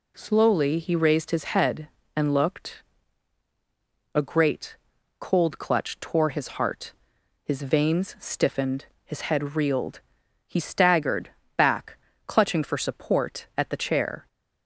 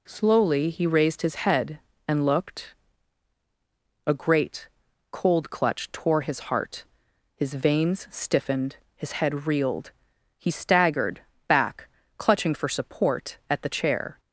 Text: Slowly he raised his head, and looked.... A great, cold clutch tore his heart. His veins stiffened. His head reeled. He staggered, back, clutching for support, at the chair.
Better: neither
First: none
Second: none

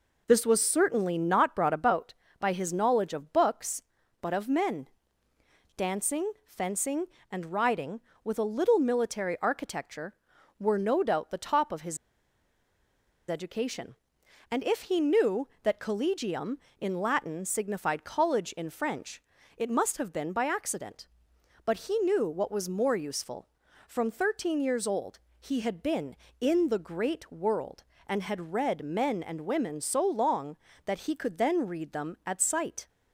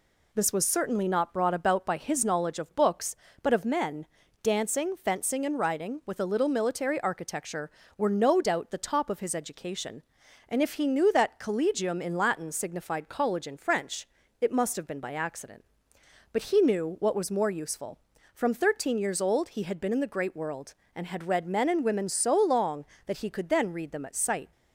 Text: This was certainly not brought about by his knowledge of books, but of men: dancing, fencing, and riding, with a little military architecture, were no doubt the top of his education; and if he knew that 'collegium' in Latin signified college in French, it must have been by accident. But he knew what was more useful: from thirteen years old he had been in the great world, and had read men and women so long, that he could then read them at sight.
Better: second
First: pauses between "his" and "education"; strong; at 11.9 s; 1.3 s long // pauses between "old" and "he"; slight; at 25.1 s; 0.20 s long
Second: none

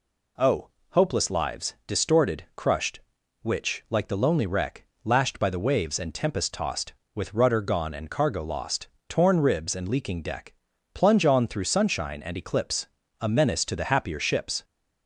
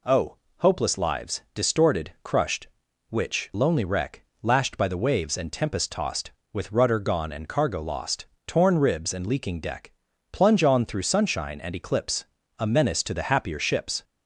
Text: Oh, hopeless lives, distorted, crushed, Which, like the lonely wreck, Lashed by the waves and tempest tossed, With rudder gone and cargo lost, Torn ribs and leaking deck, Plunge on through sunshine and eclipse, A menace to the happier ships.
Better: first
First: none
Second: skips "like the"; at 3.5 s

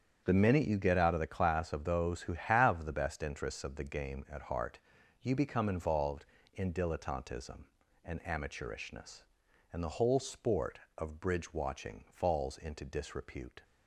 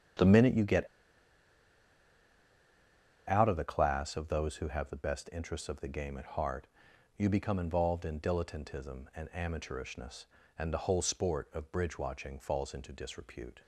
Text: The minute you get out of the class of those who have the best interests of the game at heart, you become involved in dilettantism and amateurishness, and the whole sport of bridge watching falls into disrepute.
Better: first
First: starts louder than the rest; strong; until 1.2 s; 8 dB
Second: starts louder than the rest; strong; until 3.6 s; 8.5 dB // pauses between "get" and "out"; strong; at 0.8 s; 2.4 s long

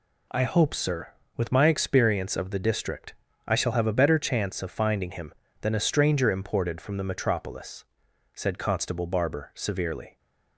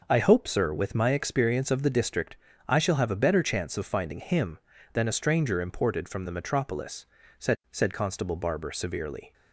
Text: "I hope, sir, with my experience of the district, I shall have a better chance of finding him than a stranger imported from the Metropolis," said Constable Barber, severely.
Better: first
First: none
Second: starts louder than the rest; noticeable; until 1.0 s; 6 dB // says "said" twice; at 7.7 s

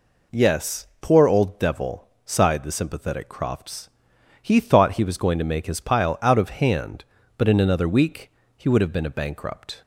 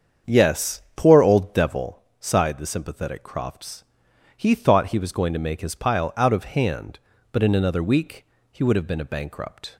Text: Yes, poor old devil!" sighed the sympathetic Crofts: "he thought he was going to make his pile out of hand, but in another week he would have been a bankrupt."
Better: first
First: pauses between "week" and "he"; slight; at 8.2 s; 0.26 s long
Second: starts louder than the rest; strong; until 1.9 s; 7.5 dB // pauses between "week" and "he"; slight; at 8.2 s; 0.26 s long

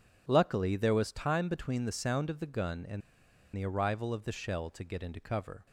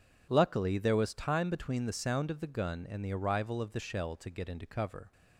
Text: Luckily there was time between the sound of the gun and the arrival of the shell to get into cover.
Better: second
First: pauses between "and" and "the"; noticeable; at 3.0 s; 0.54 s long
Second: none

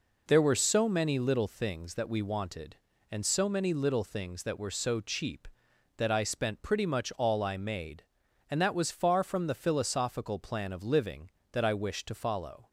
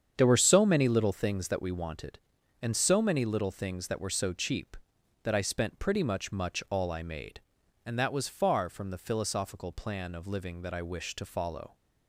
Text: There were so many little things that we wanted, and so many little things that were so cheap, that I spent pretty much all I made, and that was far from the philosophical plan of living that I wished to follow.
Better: first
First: none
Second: starts louder than the rest; strong; until 1.1 s; 7.5 dB // says "much" twice; at 6.3 s

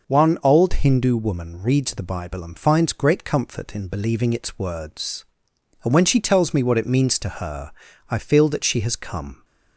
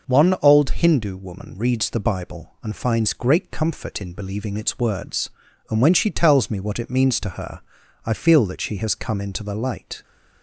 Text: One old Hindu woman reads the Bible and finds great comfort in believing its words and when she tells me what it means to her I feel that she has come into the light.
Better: second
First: pauses between "her" and "I"; at 7.7 s; 0.40 s long // stops before "into the light"; at 9.4 s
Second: pauses between "her" and "I"; at 7.6 s; 0.44 s long

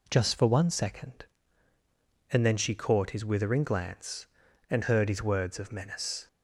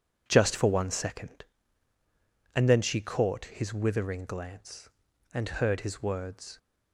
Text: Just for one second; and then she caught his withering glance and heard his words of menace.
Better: first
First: none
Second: stops before "of menace"; at 6.5 s

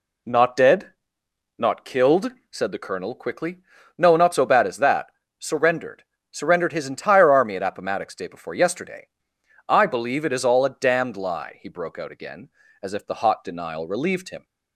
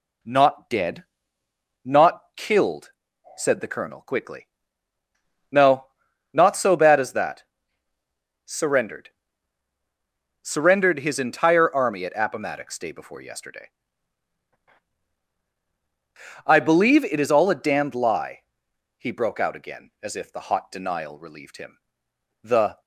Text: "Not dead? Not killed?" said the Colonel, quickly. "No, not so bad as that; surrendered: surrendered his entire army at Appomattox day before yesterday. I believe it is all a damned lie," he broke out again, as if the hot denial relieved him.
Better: first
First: none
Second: goes on to say "The"; slight; from 22.4 s on; 0.38 s long

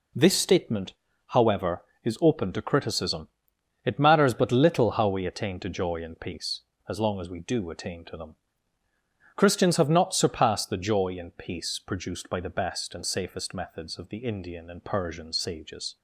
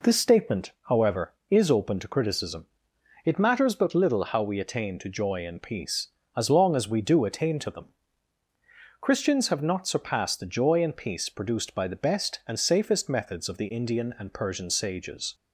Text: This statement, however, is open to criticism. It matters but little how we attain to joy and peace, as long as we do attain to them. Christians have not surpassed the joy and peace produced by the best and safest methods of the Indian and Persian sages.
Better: neither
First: none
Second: none

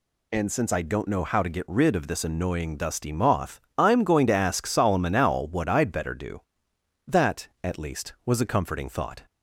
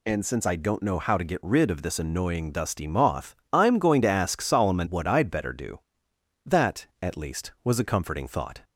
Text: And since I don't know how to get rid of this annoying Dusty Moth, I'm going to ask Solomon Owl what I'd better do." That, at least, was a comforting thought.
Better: first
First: none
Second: skips "Owl"; at 4.8 s

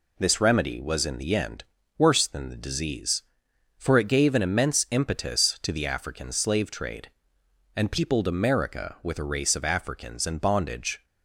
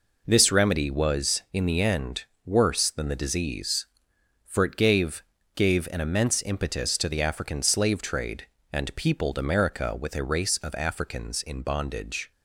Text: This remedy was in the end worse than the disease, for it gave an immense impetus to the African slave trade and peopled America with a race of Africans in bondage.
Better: first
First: pauses between "end" and "worse"; slight; at 1.6 s; 0.32 s long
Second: pauses between "end" and "worse"; slight; at 2.2 s; 0.22 s long // says "gave" twice; at 5.5 s

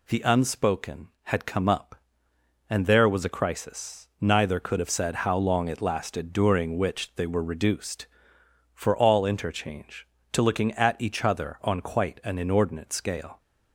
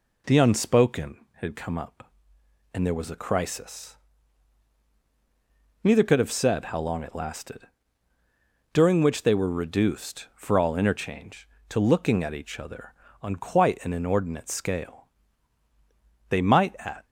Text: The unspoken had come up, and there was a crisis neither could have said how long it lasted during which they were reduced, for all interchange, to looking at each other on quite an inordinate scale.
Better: first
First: none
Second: pauses between "crisis" and "neither"; strong; at 3.9 s; 1.9 s long // pauses between "lasted" and "during"; at 7.5 s; 1.1 s long // goes on to say "They might at"; noticeable; from 16.3 s on; 0.74 s long

